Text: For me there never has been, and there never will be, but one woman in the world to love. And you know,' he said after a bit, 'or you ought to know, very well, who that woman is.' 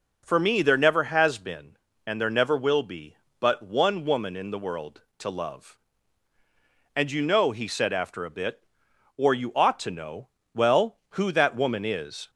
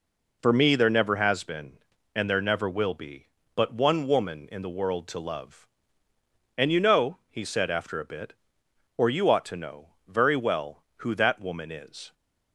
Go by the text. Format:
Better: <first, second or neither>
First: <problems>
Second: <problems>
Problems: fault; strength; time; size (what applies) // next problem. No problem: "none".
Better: second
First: skips "very"; at 10.4 s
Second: none